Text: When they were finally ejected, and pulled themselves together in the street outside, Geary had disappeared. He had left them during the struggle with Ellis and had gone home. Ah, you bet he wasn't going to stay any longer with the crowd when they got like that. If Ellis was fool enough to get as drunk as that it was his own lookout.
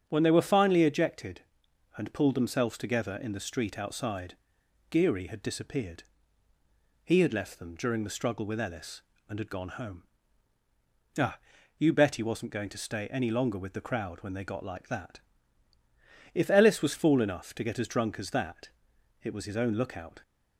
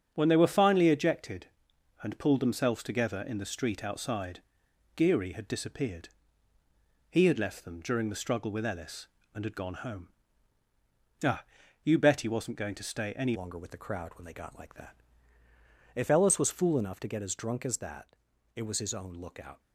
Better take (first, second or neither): first